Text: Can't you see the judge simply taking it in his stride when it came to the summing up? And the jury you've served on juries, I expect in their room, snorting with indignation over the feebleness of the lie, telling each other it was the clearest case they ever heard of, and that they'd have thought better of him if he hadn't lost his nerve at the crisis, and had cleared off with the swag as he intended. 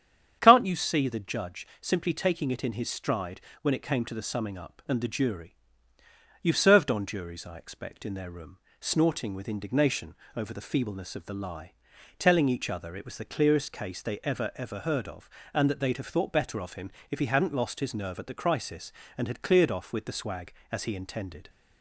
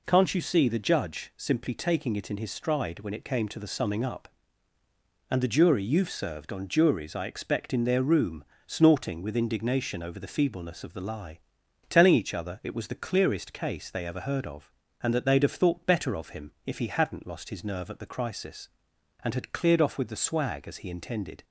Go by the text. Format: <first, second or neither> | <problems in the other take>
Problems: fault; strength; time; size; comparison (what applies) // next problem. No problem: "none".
second | starts louder than the rest; strong; until 1.4 s; 9 dB // pauses between "judge" and "simply"; slight; at 1.6 s; 0.16 s long // pauses between "stride" and "when"; slight; at 3.4 s; 0.20 s long // pauses between "jury" and "you've"; noticeable; at 5.5 s; 0.86 s long // pauses between "indignation" and "over"; slight; at 10.1 s; 0.20 s long // says "ever" twice; at 14.5 s // pauses between "him" and "if"; slight; at 16.9 s; 0.18 s long